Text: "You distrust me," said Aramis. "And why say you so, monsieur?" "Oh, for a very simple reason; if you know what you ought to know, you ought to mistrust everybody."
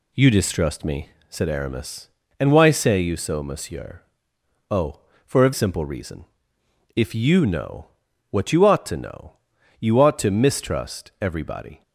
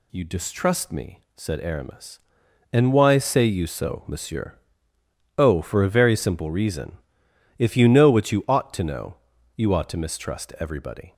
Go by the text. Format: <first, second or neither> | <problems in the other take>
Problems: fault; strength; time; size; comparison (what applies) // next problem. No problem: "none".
second | skips "very"; at 5.5 s // pauses between "know" and "what"; at 7.8 s; 0.44 s long